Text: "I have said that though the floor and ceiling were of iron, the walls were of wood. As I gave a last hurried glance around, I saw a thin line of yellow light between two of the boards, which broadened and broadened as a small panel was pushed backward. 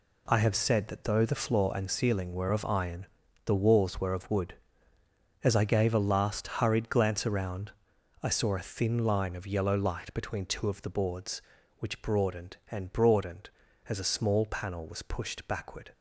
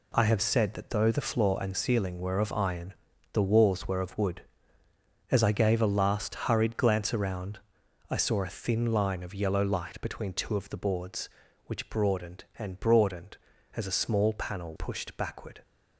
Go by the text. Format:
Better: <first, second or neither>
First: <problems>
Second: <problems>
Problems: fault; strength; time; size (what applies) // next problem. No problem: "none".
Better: first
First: none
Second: skips "was"; at 14.7 s